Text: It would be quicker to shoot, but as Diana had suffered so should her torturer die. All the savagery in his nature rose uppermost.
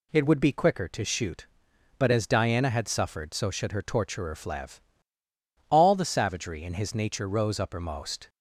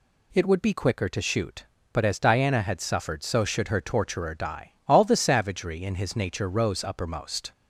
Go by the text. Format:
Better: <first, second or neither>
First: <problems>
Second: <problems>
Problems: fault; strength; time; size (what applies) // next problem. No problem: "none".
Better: second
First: says "flev" for "die"; at 4.3 s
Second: none